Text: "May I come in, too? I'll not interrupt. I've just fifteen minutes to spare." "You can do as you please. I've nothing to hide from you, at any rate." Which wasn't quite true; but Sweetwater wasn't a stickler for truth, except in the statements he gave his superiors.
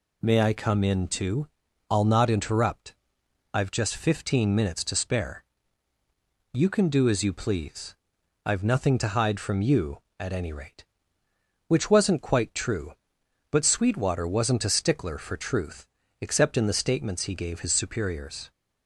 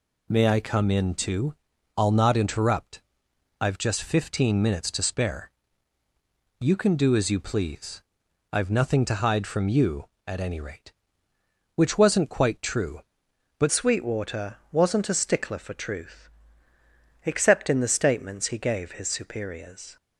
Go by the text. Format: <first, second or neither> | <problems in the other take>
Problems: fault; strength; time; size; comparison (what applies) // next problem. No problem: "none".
first | changes voice at "Sweetwater"; from 13.7 s on; 6.2 s long